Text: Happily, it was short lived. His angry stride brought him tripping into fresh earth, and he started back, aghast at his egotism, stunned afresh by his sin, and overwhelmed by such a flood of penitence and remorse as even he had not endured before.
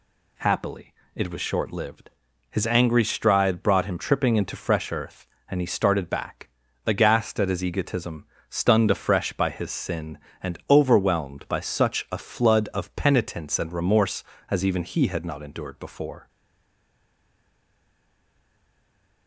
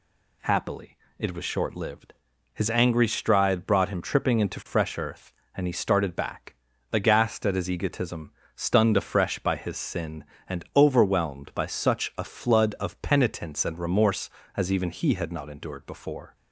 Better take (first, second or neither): second